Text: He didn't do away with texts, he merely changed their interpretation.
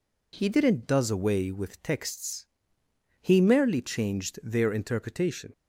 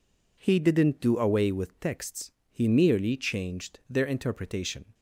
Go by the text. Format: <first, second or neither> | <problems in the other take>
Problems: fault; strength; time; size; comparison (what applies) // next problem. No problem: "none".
second | says "does" for "do"; at 0.8 s